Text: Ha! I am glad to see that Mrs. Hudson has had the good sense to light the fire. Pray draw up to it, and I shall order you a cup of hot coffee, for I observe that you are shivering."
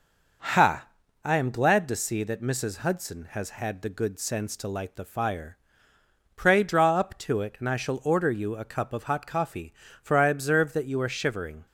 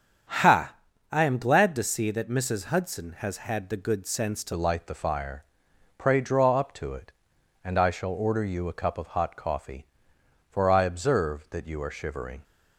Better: first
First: none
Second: starts louder than the rest; strong; until 1.7 s; 7.5 dB // changes voice at "light"; from 4.5 s on; 7.9 s long

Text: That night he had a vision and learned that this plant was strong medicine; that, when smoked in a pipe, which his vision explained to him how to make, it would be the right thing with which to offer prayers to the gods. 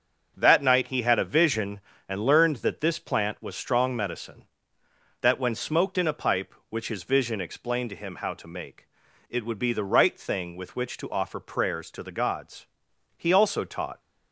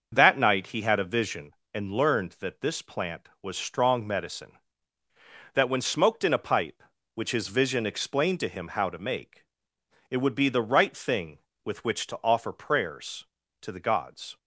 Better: second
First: starts louder than the rest; until 1.3 s; 6.5 dB // goes on to say "He also taught"; noticeable; from 13.1 s on; 0.82 s long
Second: starts louder than the rest; until 1.1 s; 6.5 dB

